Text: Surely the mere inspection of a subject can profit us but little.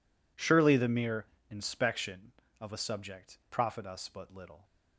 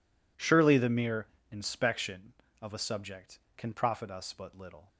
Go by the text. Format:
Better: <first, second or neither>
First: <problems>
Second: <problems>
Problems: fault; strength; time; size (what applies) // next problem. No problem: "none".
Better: second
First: pauses between "mere" and "inspection"; slight; at 1.2 s; 0.24 s long // skips "can"; at 3.4 s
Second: pauses between "mere" and "inspection"; slight; at 1.2 s; 0.24 s long